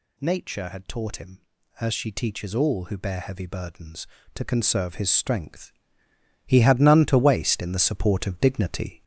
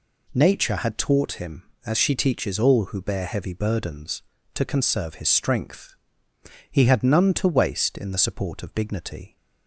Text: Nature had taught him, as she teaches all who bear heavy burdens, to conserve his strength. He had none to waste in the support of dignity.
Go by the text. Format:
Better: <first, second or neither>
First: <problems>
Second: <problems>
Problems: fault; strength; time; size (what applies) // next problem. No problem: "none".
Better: second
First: gets louder; noticeable; throughout; 5 dB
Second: none